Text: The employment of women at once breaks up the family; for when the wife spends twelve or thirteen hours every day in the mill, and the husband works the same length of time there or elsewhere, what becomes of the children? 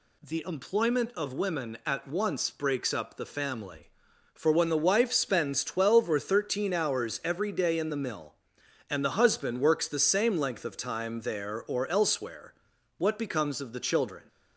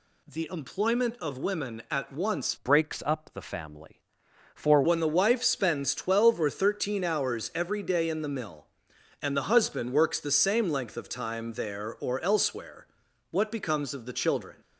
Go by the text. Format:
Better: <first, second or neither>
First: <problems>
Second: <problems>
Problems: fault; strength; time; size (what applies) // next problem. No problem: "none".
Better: first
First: none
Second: changes voice from "breaks" to "for"; from 2.5 to 4.8 s; 2.3 s long